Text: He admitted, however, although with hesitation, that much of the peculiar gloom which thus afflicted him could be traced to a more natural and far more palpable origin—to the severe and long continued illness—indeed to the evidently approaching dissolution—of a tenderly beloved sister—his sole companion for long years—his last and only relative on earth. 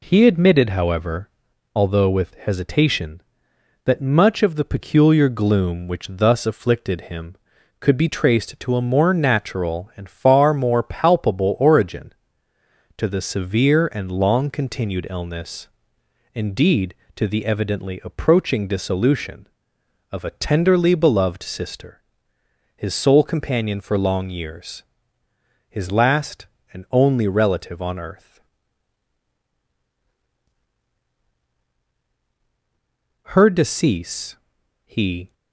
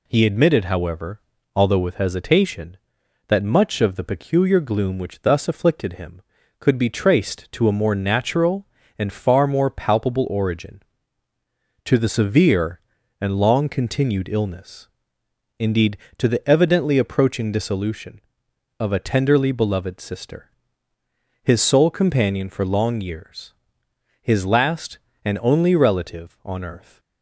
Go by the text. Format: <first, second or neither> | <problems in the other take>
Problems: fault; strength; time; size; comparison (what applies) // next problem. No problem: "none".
second | goes on to say "Her decease he"; strong; from 33.2 s on; 2.0 s long